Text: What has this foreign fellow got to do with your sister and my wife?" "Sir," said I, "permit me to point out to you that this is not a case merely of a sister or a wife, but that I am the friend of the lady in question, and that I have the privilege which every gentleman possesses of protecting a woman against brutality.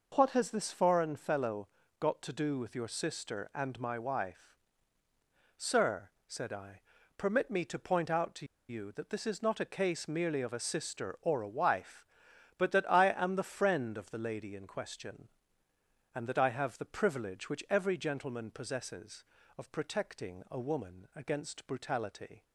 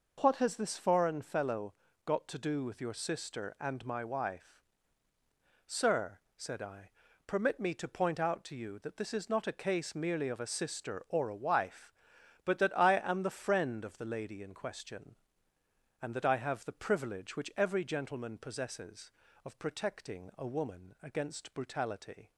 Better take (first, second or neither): second